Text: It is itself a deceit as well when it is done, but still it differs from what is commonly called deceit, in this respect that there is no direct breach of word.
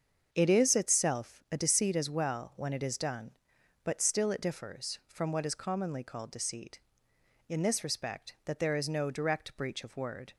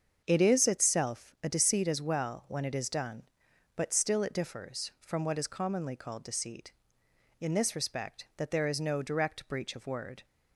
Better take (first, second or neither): neither